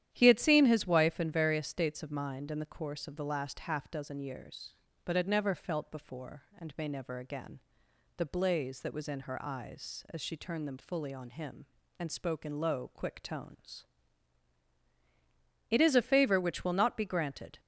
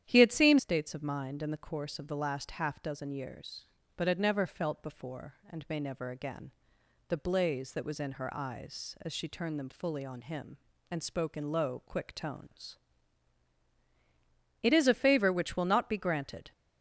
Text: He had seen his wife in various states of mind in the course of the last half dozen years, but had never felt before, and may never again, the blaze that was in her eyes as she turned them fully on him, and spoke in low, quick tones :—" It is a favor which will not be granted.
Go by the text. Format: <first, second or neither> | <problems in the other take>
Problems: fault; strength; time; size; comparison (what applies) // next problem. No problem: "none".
first | starts louder than the rest; strong; until 1.0 s; 10 dB; strong in the first // skips "his wife in various"; at 0.5 s